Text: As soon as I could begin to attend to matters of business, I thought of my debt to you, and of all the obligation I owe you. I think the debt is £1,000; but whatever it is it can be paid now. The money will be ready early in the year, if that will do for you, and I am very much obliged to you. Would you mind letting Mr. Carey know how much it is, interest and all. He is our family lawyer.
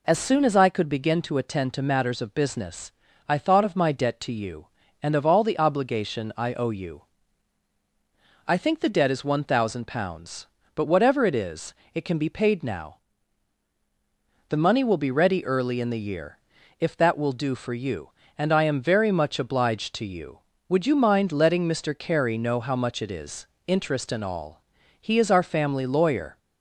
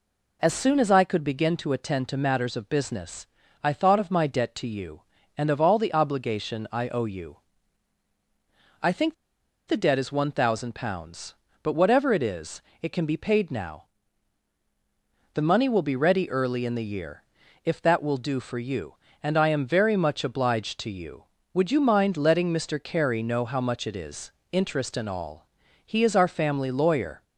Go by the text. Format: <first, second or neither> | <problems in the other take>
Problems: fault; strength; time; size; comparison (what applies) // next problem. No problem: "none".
first | pauses between "think" and "the"; noticeable; at 9.1 s; 0.54 s long // pauses between "is" and "it"; slight; at 12.6 s; 0.22 s long; slight in the first